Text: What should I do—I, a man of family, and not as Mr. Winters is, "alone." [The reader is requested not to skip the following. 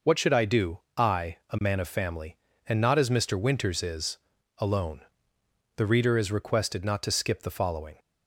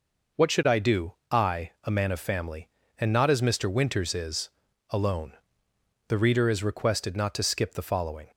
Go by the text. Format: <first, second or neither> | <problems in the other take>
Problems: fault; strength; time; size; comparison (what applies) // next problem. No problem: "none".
neither | none